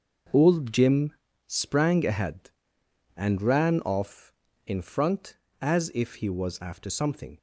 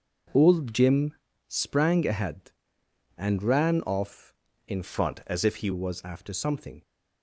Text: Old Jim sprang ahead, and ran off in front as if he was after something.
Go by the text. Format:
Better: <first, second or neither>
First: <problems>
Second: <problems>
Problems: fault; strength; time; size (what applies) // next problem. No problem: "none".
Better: first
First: starts louder than the rest; until 1.6 s; 6 dB // pauses between "Jim" and "sprang"; slight; at 1.1 s; 0.32 s long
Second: starts louder than the rest; noticeable; until 1.6 s; 6 dB // pauses between "Jim" and "sprang"; slight; at 1.1 s; 0.32 s long // changes voice from "front" to "he"; from 4.8 to 5.6 s; 0.8 s long